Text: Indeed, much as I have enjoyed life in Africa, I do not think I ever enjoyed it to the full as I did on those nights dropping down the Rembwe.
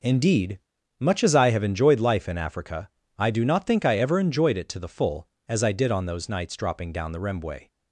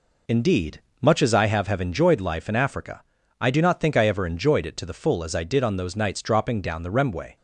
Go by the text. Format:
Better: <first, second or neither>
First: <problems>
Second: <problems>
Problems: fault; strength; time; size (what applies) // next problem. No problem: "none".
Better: first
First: none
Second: says "have" twice; at 1.6 s